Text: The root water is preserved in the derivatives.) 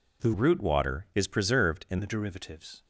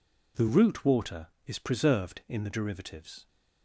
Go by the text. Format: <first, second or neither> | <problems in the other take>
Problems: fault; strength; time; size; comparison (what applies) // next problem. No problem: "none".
second | changes voice from "root" to "in"; from 0.3 to 1.9 s; 1.6 s long